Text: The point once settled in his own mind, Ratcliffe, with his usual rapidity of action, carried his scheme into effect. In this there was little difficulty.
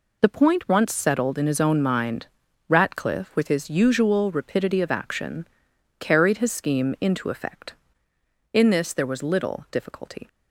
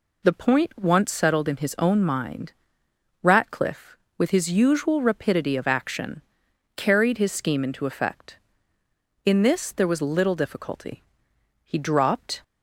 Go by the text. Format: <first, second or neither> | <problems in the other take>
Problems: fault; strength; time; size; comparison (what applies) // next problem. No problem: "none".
first | goes on to say "He dropped"; noticeable; from 11.6 s on; 0.80 s long